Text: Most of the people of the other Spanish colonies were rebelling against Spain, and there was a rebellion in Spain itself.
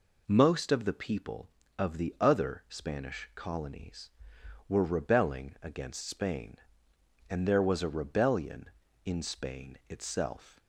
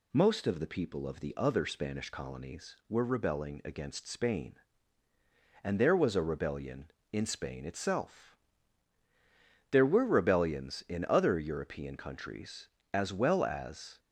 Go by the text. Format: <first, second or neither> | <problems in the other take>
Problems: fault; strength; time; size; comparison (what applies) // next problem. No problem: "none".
first | goes on to say "There were rebellions in other European countries as well as"; strong; from 9.6 s on; 4.3 s long